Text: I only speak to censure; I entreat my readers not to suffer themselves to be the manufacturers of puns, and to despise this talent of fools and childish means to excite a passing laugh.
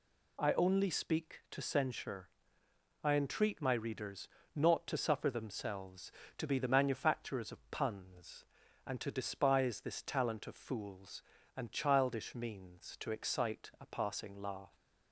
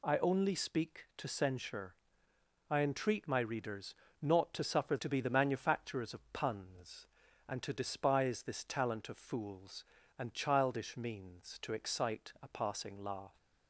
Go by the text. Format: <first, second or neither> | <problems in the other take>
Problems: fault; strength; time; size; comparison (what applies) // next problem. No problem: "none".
first | pauses between "readers" and "not"; slight; at 3.9 s; 0.26 s long; slight in the first // skips "themselves"; at 4.9 s